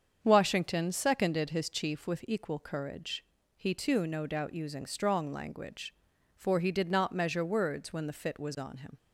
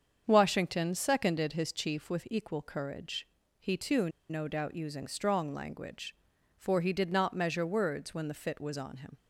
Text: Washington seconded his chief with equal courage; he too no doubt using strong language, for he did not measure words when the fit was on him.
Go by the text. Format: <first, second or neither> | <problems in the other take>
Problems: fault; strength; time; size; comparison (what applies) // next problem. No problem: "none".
first | starts louder than the rest; strong; until 1.2 s; 7.5 dB; strong in the first // pauses between "too" and "no"; slight; at 4.0 s; 0.21 s long